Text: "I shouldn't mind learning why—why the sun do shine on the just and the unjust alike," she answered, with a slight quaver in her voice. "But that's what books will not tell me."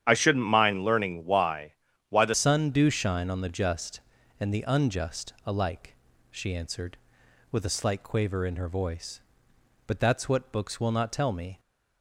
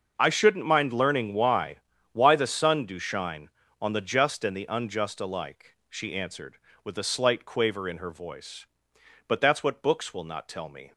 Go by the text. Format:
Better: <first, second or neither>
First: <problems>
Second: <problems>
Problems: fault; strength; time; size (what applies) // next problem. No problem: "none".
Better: second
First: starts louder than the rest; strong; until 1.0 s; 10 dB // changes voice at "sun"; from 2.3 s on; 9.2 s long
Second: none